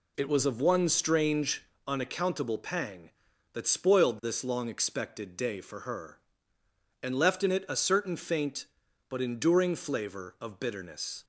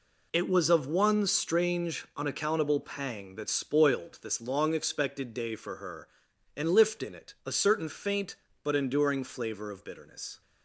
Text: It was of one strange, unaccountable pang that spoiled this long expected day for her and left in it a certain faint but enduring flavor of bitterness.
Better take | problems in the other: first | says "lift" for "left"; at 6.6 s

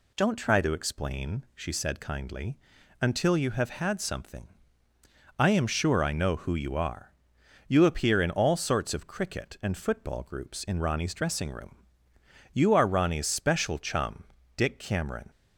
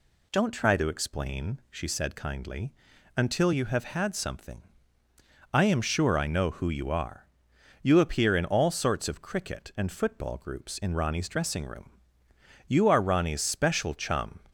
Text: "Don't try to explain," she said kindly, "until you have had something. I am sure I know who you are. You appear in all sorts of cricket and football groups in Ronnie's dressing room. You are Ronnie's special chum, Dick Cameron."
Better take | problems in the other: first | stops before "Dick Cameron"; at 14.4 s

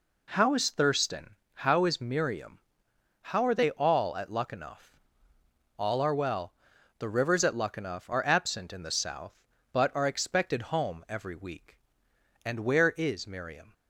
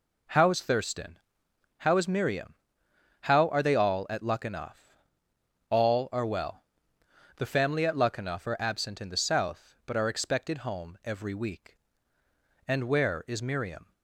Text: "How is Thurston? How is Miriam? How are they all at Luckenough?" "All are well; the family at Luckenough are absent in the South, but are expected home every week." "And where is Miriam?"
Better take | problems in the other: second | says "rivers" for "family"; at 7.0 s

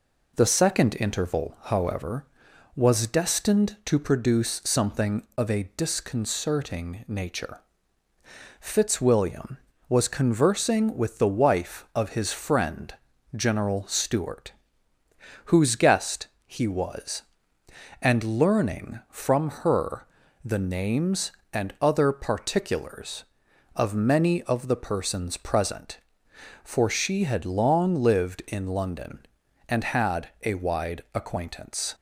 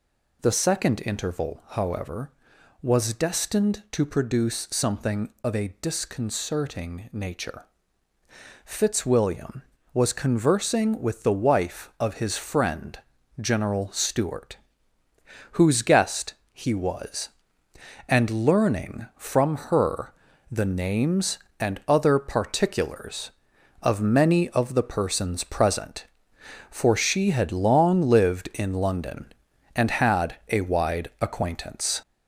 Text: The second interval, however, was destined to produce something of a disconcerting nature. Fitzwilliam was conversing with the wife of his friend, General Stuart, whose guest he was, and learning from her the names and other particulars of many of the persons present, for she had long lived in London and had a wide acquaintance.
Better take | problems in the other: first | gets louder; noticeable; throughout; 4.5 dB // pauses between "guest" and "he"; slight; at 16.3 s; 0.18 s long; slight in the first // pauses between "her" and "the"; at 20.1 s; 0.38 s long; also in the first

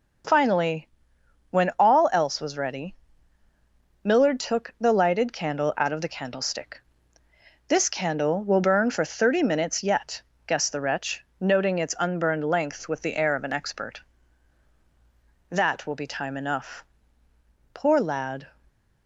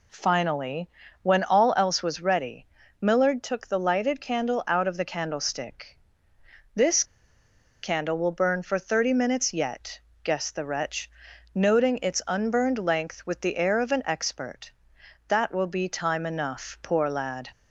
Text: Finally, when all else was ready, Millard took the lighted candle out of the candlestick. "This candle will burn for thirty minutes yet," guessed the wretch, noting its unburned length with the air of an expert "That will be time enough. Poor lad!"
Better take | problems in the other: first | pauses between "This" and "candle"; noticeable; at 7.0 s; 0.79 s long

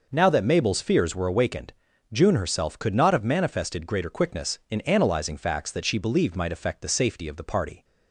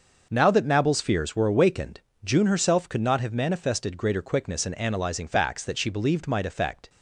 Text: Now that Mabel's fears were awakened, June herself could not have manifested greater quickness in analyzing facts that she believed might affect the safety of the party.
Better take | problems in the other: first | starts louder than the rest; until 1.3 s; 6 dB // stops before "the safety of the party"; at 6.8 s

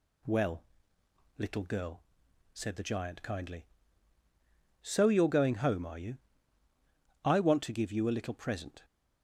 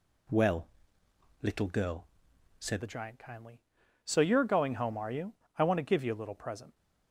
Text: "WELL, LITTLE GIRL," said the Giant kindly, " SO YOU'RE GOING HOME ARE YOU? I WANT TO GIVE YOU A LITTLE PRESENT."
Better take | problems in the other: first | changes voice at "the"; from 2.8 s on; 3.9 s long

